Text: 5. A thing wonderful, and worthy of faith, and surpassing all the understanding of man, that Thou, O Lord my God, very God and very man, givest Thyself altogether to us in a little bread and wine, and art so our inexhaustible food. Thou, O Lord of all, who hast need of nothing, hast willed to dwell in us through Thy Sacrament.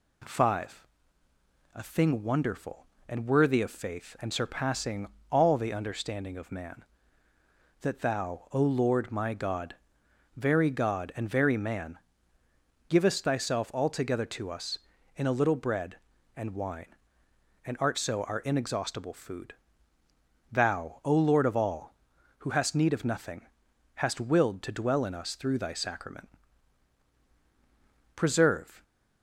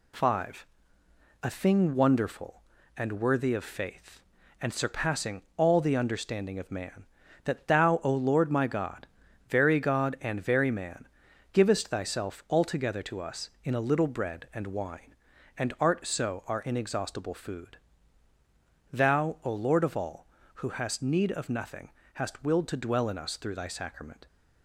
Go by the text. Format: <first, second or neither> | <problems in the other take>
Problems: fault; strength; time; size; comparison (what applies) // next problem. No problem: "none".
second | pauses between "surpassing" and "all"; slight; at 5.0 s; 0.22 s long // goes on to say "Preserve"; noticeable; from 28.1 s on; 0.68 s long